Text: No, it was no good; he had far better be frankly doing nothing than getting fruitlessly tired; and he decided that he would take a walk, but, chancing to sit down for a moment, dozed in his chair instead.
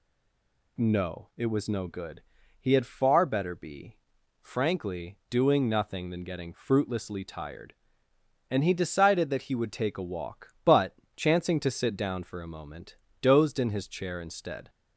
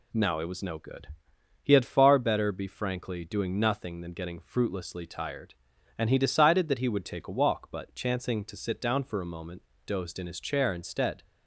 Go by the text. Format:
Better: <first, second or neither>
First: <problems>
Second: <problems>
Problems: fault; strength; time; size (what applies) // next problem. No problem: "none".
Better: second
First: stays silent before the first word; slight; until 0.7 s; 0.7 s long // pauses between "be" and "frankly"; noticeable; at 3.9 s; 0.48 s long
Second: none